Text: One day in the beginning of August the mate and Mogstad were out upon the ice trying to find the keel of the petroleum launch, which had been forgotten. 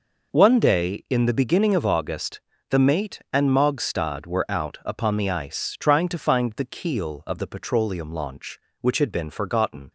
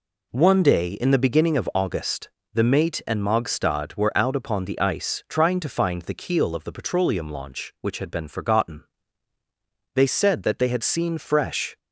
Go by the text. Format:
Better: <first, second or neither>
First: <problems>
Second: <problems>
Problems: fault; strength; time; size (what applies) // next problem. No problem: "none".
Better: first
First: pauses between "August" and "the"; slight; at 2.4 s; 0.26 s long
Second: pauses between "August" and "the"; slight; at 2.2 s; 0.26 s long // goes on to say "They said that they had seen fresh"; strong; from 9.9 s on; 1.8 s long